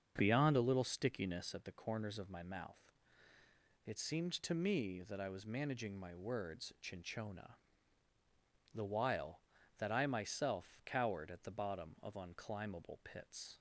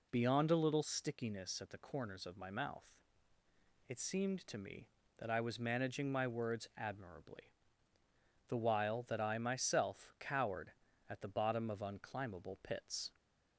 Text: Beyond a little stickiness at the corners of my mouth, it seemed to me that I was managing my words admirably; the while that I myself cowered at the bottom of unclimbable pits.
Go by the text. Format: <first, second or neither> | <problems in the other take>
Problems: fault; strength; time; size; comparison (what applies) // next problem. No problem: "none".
second | starts louder than the rest; until 1.1 s; 7 dB // says "chinchona" for "admirably"; at 6.8 s